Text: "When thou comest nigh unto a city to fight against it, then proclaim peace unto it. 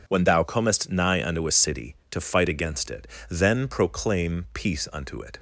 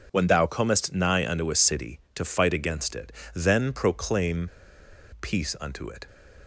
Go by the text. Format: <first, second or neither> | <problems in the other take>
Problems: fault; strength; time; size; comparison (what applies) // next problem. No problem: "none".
first | pauses between "proclaim" and "peace"; noticeable; at 4.4 s; 0.71 s long